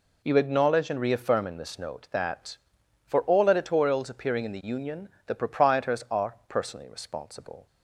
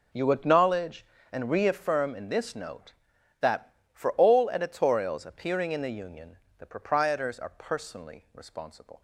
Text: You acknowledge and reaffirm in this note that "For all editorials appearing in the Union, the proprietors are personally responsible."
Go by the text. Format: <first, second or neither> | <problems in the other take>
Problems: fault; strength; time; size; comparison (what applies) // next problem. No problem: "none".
neither | none